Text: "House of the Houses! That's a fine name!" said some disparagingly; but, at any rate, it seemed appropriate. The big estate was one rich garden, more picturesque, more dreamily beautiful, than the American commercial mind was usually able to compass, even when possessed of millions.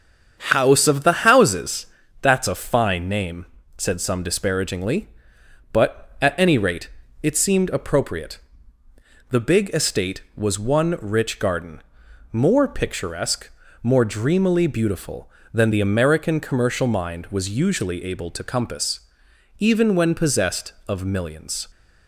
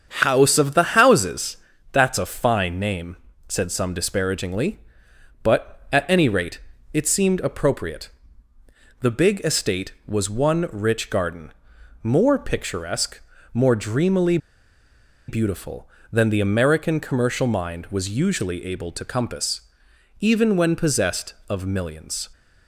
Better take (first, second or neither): first